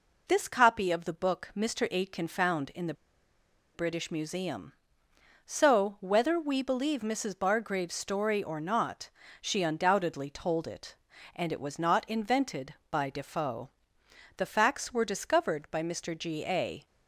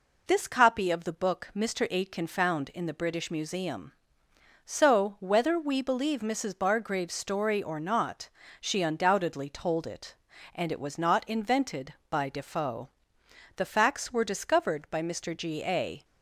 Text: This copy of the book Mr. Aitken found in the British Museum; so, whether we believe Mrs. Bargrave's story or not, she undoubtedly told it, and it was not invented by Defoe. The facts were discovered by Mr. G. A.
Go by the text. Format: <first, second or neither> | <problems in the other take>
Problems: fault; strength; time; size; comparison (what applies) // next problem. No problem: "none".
second | pauses between "the" and "British"; noticeable; at 2.9 s; 0.81 s long